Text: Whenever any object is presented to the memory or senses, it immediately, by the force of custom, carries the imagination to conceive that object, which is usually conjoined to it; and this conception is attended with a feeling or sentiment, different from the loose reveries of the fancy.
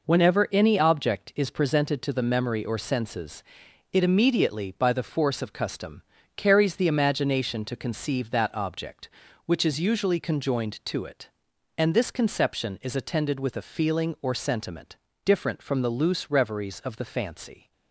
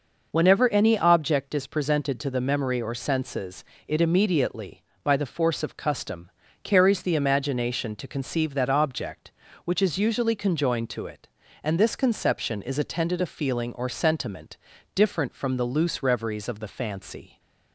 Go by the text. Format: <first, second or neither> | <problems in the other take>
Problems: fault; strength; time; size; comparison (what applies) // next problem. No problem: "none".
first | skips "with"; at 13.2 s